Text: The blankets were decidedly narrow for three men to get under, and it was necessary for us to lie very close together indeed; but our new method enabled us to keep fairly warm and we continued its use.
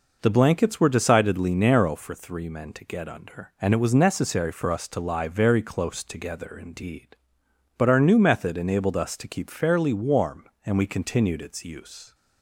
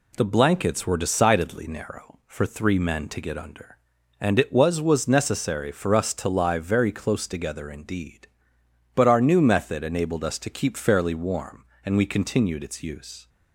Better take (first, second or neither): first